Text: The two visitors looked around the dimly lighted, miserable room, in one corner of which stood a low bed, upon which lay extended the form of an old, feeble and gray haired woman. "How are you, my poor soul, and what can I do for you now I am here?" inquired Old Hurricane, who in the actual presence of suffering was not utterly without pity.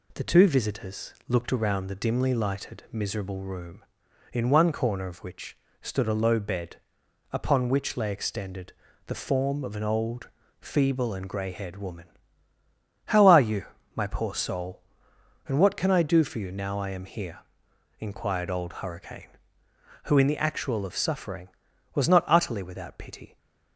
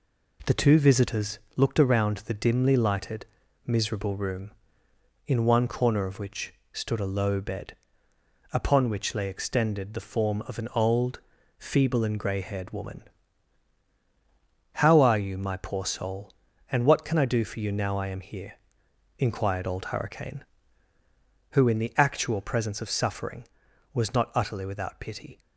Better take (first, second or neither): second